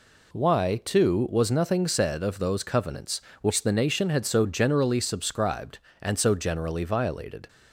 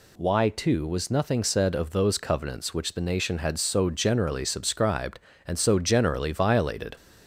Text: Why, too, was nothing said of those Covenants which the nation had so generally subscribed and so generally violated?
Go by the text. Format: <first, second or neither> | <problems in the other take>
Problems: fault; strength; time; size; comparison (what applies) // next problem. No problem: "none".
neither | none